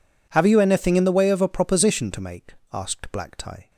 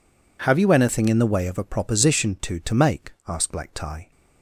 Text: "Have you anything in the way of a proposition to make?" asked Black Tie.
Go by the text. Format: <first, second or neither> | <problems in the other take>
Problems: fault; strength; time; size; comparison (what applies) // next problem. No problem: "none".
first | says "to" twice; at 2.6 s